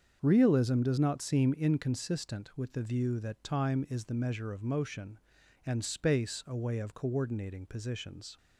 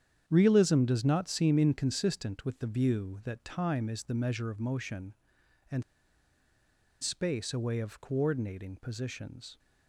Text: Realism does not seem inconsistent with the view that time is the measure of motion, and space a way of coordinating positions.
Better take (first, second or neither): first